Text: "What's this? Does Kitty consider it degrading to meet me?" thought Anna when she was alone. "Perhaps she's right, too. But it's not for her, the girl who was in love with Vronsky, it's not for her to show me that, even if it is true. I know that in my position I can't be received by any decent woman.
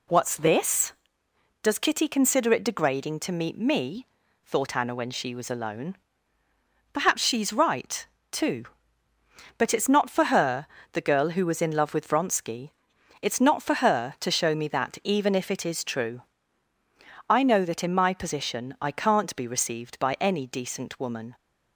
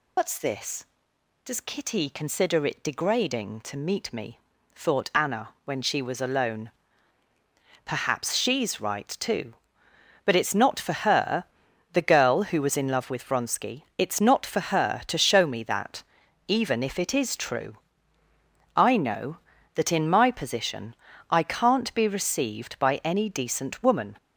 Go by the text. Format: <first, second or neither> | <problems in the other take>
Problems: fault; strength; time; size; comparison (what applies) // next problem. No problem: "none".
first | loses the start of "What's"; at 0.1 s; 85 ms // pauses between "Anna" and "when"; slight; at 5.4 s; 0.16 s long // pauses between "position" and "I"; slight; at 20.9 s; 0.34 s long